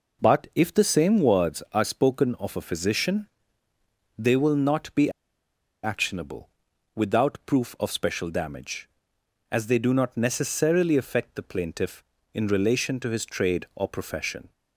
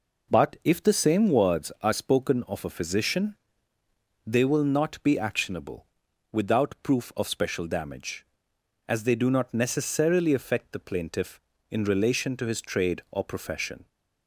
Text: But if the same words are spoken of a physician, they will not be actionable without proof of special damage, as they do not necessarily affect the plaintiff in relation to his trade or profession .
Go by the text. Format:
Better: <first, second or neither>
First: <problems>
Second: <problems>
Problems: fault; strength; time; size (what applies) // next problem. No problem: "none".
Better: second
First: pauses between "be" and "actionable"; noticeable; at 5.1 s; 0.73 s long // pauses between "actionable" and "without"; noticeable; at 6.4 s; 0.46 s long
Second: pauses between "actionable" and "without"; noticeable; at 5.8 s; 0.46 s long